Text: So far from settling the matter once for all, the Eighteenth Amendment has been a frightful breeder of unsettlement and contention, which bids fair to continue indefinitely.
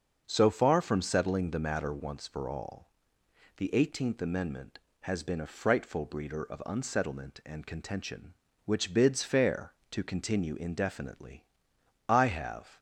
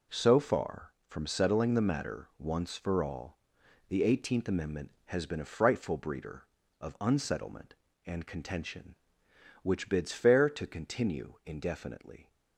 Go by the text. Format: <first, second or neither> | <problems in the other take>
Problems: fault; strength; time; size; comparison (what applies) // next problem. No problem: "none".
second | starts louder than the rest; until 1.2 s; 6.5 dB // goes on to say "I have"; noticeable; from 12.0 s on; 0.70 s long